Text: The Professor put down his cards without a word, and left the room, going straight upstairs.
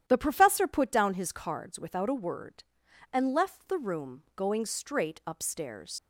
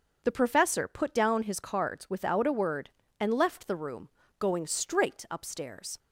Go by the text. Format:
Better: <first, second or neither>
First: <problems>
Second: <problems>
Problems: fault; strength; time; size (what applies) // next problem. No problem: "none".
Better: second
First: starts louder than the rest; strong; until 1.0 s; 11 dB // leaves "upstairs" unfinished; at 5.9 s; 60 ms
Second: starts louder than the rest; until 1.2 s; 6.5 dB